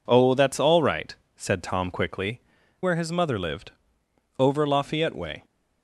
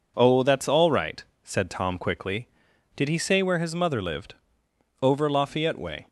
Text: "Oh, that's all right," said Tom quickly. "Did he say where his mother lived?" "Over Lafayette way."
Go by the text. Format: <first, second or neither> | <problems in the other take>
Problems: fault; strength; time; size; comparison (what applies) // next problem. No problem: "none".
second | skips "Did he say"; at 2.6 s